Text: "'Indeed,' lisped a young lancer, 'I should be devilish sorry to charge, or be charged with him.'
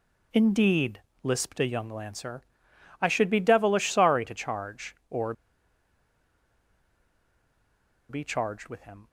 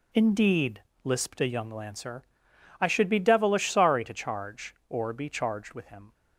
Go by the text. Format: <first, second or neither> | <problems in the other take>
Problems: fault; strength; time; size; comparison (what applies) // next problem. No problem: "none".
second | pauses between "or" and "be"; strong; at 5.3 s; 2.7 s long